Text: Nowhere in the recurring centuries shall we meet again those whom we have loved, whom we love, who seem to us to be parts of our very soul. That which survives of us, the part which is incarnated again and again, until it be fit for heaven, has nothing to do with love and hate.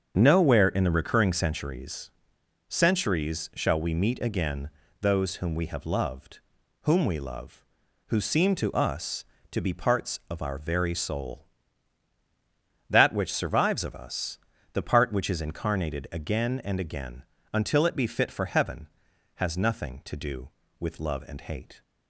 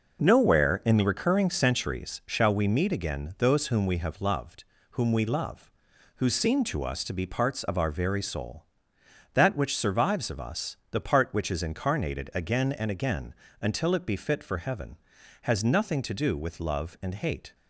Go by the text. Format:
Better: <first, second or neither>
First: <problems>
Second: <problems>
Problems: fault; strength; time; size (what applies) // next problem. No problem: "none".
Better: second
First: starts louder than the rest; strong; until 1.1 s; 7 dB // says "centuries" twice; at 2.6 s // pauses between "again" and "those"; slight; at 4.6 s; 0.32 s long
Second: none